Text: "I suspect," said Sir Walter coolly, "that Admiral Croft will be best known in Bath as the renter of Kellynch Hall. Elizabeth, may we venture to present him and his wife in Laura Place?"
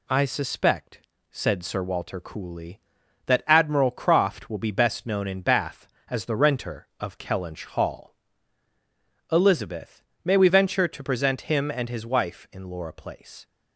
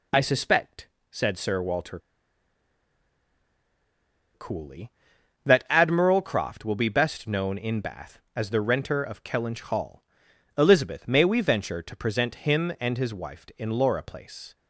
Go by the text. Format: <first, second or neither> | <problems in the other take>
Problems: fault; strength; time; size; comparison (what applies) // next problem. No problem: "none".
first | pauses between "Walter" and "coolly"; strong; at 1.9 s; 2.3 s long